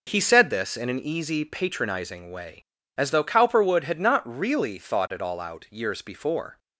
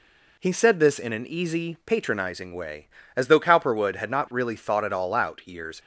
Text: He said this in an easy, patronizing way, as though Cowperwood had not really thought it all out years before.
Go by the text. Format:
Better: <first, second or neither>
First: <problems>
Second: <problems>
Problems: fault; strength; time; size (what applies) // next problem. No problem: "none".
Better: first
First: none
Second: stops before "before"; at 5.7 s